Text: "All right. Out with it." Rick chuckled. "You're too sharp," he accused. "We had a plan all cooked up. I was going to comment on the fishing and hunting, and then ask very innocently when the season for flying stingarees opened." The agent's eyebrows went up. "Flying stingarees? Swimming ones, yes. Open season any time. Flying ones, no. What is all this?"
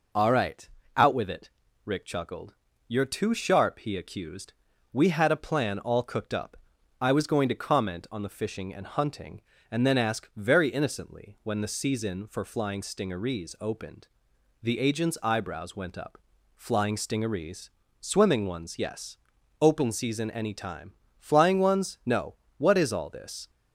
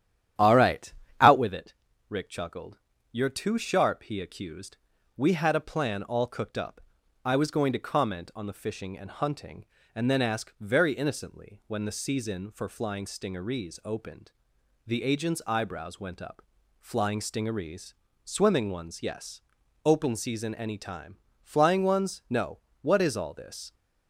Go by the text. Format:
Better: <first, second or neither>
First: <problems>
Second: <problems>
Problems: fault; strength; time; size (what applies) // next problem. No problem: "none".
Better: first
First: none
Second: starts louder than the rest; strong; until 1.5 s; 11 dB